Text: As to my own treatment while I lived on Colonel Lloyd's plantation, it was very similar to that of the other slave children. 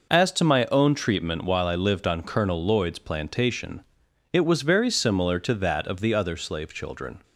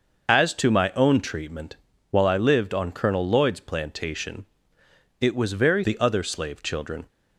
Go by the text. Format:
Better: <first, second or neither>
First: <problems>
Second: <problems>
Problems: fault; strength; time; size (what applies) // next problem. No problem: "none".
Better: first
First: none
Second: pauses between "treatment" and "while"; slight; at 1.7 s; 0.34 s long // skips "similar to that of"; at 5.8 s